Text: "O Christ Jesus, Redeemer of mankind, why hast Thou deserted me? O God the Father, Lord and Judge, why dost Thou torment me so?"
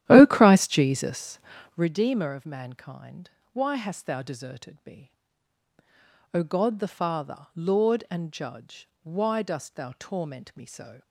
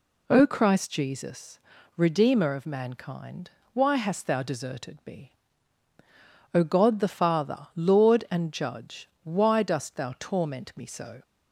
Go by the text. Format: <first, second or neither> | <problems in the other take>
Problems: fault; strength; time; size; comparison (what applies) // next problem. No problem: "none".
second | starts louder than the rest; strong; until 1.9 s; 12.5 dB